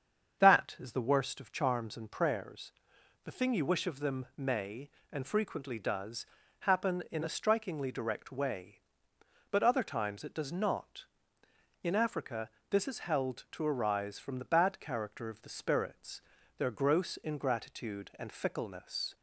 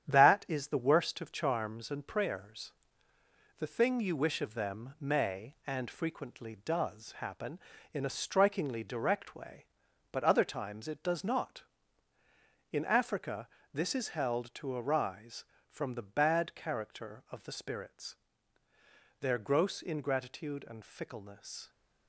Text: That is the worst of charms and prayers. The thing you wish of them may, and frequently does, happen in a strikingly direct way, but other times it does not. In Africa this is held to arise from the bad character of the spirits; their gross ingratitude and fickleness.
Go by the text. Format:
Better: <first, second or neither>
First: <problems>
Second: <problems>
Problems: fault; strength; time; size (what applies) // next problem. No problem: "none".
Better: first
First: starts louder than the rest; strong; until 1.4 s; 7.5 dB // pauses between "Africa" and "this"; slight; at 12.4 s; 0.20 s long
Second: gets quieter; noticeable; throughout; 5.5 dB // starts louder than the rest; strong; until 1.1 s; 9.5 dB // pauses between "Africa" and "this"; slight; at 13.4 s; 0.26 s long